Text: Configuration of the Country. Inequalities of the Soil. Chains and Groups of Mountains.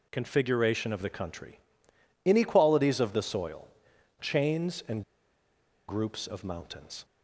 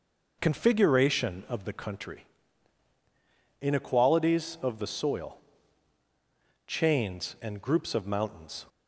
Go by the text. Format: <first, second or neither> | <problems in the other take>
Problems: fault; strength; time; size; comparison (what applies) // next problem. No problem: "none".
second | pauses between "and" and "Groups"; noticeable; at 5.0 s; 0.86 s long